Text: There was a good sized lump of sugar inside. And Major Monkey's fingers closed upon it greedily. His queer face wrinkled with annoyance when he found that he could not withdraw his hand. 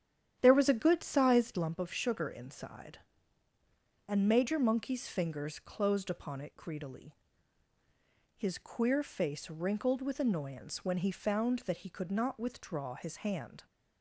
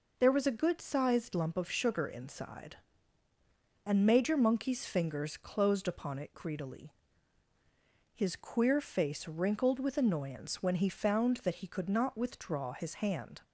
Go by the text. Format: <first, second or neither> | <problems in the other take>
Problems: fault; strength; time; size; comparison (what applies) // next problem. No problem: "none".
second | starts louder than the rest; strong; until 1.7 s; 10 dB